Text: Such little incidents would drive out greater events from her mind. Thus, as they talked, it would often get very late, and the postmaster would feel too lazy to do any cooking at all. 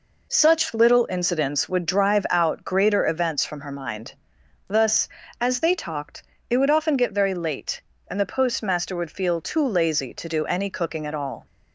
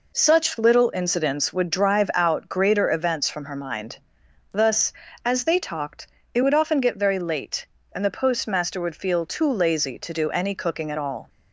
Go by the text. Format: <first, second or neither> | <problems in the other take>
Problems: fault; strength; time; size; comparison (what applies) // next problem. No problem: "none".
neither | none